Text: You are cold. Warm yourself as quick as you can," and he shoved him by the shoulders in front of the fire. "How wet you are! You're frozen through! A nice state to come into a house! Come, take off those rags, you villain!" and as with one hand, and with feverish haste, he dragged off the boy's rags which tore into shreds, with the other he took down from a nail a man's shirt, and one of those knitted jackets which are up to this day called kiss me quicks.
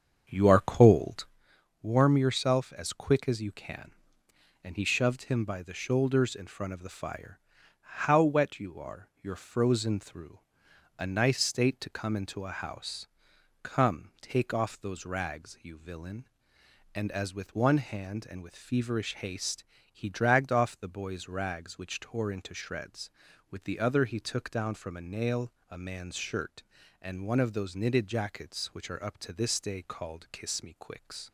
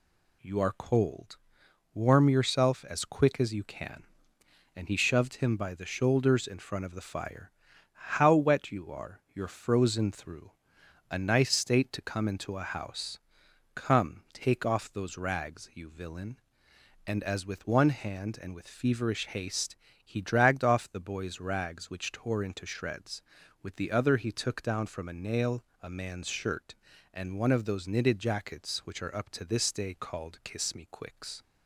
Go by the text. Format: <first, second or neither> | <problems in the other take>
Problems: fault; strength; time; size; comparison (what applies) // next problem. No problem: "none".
second | starts louder than the rest; strong; until 1.4 s; 7.5 dB // pauses between "nail" and "a"; slight; at 25.5 s; 0.18 s long; slight in the second